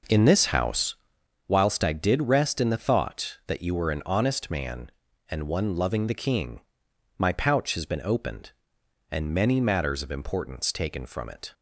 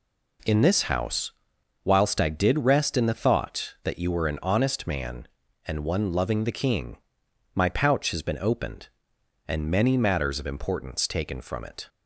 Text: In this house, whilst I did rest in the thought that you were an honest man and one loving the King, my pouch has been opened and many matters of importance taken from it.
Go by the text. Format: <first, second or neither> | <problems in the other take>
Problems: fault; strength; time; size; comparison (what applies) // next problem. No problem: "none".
second | starts louder than the rest; noticeable; until 1.3 s; 5.5 dB